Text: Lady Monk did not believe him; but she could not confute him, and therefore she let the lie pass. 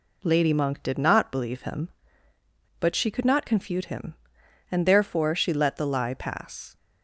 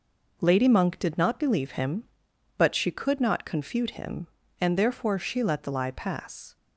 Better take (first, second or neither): neither